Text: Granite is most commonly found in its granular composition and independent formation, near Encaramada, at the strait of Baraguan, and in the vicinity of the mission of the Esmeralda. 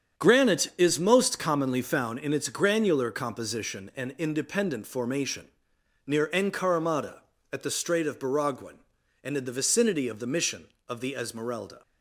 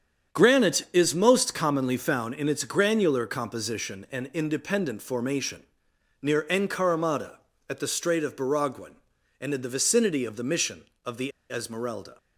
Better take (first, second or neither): first